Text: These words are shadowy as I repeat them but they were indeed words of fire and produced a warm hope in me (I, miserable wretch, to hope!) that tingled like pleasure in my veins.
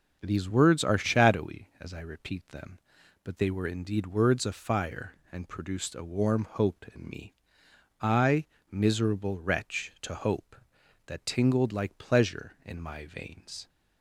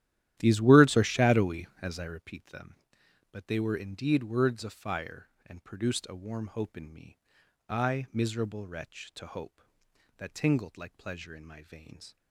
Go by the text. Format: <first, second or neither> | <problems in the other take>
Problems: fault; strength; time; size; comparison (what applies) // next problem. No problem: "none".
first | starts louder than the rest; strong; until 2.3 s; 12.5 dB